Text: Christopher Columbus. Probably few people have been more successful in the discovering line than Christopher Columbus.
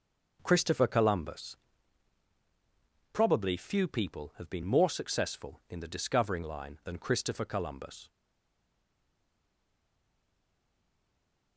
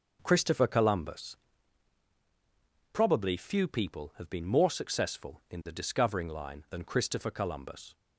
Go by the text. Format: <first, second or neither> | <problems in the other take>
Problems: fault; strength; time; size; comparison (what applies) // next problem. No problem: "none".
second | starts louder than the rest; noticeable; until 1.4 s; 6 dB; noticeable in the second // stays silent after the last word; strong; from 8.0 s on; 3.5 s long